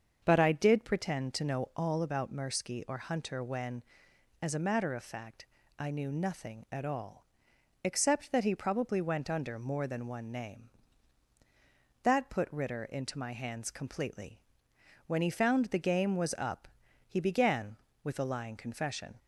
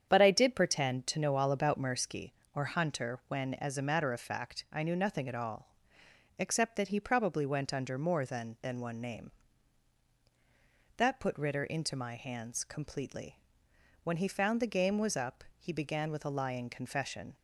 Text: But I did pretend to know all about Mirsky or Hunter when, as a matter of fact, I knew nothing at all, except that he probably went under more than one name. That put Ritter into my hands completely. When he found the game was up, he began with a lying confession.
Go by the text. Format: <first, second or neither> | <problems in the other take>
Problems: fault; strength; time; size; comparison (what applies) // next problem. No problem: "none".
first | starts louder than the rest; strong; until 1.1 s; 8.5 dB; also in the first // says "than" twice; at 8.6 s